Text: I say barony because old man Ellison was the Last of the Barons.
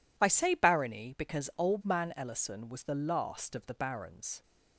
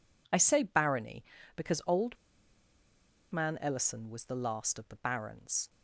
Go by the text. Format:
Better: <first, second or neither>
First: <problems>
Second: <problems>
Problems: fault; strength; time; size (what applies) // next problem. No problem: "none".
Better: first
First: none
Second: pauses between "old" and "man"; at 2.1 s; 1.1 s long